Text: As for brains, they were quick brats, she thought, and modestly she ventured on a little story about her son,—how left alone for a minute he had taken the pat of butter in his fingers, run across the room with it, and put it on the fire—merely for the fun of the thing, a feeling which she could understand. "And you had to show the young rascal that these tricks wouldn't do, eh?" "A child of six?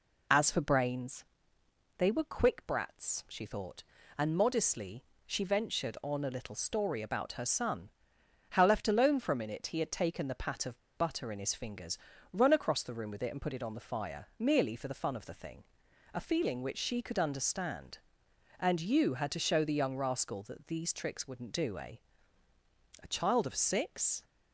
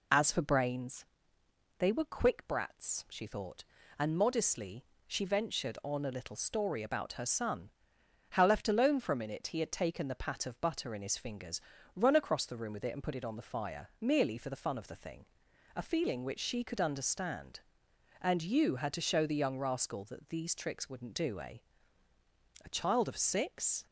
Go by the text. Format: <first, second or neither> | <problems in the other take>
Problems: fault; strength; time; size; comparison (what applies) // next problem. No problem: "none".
second | pauses between "modestly" and "she"; slight; at 5.0 s; 0.22 s long; slight in the second // pauses between "of" and "butter"; slight; at 10.7 s; 0.18 s long